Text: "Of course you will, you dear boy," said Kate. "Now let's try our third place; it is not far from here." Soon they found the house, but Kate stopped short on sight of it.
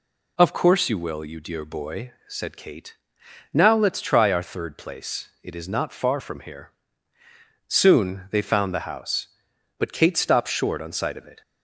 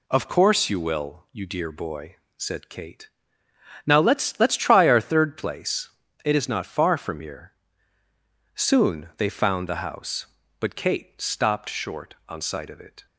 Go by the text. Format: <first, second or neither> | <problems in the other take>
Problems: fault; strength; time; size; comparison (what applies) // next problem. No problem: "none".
first | says "let's" twice; at 4.3 s